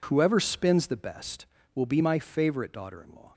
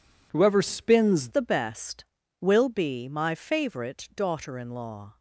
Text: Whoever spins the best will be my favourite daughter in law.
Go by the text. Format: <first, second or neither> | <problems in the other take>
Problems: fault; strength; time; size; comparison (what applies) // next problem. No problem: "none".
first | changes voice at "the"; from 1.2 s on; 3.9 s long